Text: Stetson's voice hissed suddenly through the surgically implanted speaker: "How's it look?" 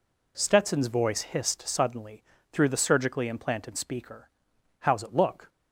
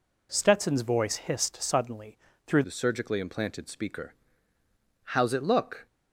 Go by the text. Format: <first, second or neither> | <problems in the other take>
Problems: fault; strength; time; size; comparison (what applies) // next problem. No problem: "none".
first | pauses between "suddenly" and "through"; slight; at 2.1 s; 0.30 s long; slight in the first // changes voice at "the"; from 2.6 s on; 3.2 s long